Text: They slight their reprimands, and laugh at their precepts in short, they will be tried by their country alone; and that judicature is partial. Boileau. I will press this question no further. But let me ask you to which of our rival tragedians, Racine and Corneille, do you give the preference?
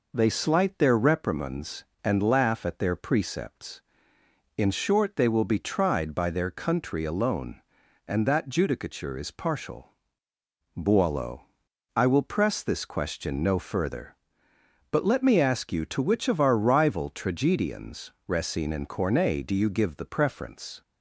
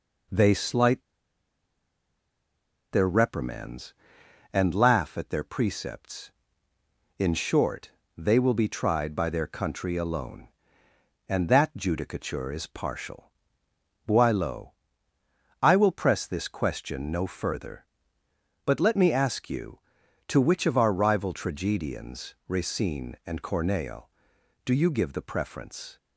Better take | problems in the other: first | pauses between "slight" and "their"; strong; at 1.0 s; 1.9 s long

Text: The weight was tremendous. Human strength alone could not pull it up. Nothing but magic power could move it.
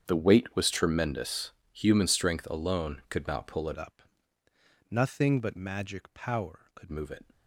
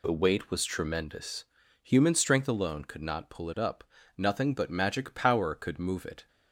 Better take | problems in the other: second | starts louder than the rest; strong; until 1.0 s; 8 dB // changes voice from "up" to "could"; from 3.7 to 6.9 s; 3.2 s long

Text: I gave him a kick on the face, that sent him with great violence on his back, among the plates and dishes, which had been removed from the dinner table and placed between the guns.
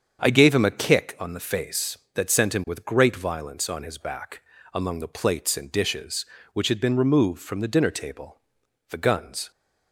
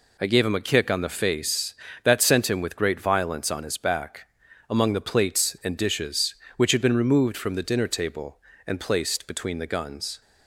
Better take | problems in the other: second | starts louder than the rest; strong; until 1.2 s; 7.5 dB // skips "and placed between"; at 8.6 s

